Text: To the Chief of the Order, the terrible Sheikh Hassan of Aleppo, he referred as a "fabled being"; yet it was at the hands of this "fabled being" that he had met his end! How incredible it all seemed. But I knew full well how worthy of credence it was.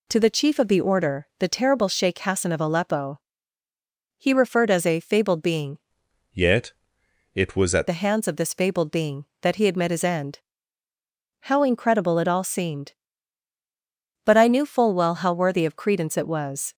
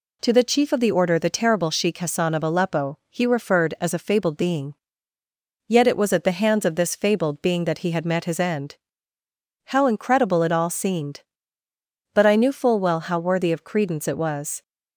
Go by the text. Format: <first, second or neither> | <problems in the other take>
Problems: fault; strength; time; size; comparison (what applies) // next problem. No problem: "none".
second | changes voice from "yet" to "at"; from 6.3 to 7.8 s; 1.5 s long // pauses between "yet" and "it"; noticeable; at 6.7 s; 0.62 s long